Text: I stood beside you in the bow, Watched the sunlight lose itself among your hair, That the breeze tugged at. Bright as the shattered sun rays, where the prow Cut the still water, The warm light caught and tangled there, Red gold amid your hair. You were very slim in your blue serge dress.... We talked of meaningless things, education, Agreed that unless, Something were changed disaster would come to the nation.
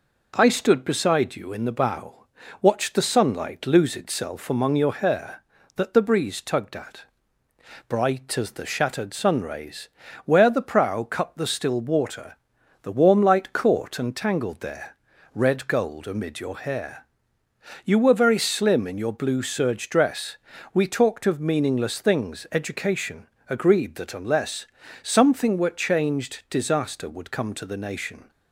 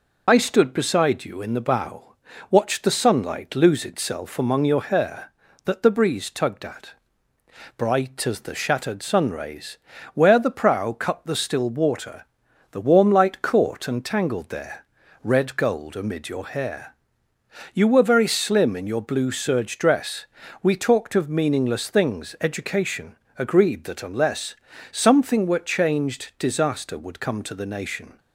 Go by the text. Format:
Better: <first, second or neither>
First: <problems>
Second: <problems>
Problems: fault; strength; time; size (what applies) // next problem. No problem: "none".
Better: first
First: none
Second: loses the start of "I"; at 0.2 s; 55 ms